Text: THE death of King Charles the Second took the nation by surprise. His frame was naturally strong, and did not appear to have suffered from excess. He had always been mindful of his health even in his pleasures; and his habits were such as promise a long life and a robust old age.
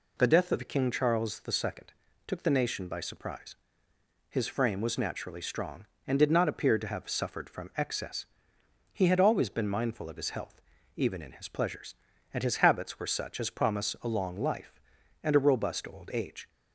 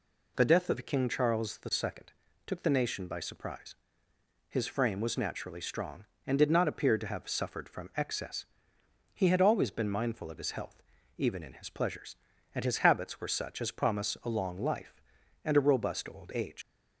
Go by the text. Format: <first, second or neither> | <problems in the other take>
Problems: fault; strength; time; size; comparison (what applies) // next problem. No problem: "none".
first | pauses between "Second" and "took"; slight; at 2.1 s; 0.34 s long; slight in the first // pauses between "health" and "even"; slight; at 10.8 s; 0.34 s long; slight in the first // leaves "age" unfinished; at 16.6 s; 75 ms